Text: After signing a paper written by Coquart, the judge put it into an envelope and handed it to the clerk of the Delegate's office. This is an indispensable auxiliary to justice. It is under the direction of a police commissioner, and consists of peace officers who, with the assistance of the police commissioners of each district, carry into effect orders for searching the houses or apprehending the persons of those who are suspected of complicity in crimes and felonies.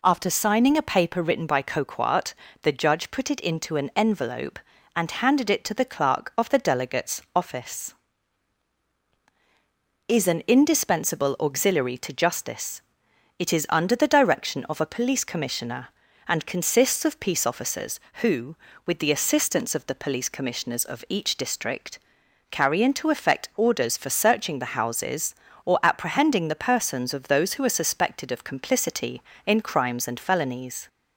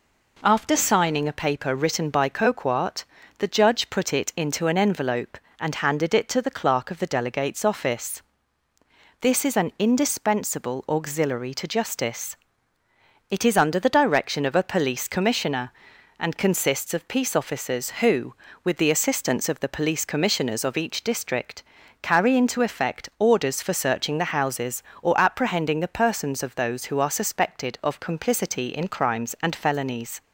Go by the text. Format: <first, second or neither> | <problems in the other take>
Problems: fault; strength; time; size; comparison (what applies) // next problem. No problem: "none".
second | skips "This"; at 9.0 s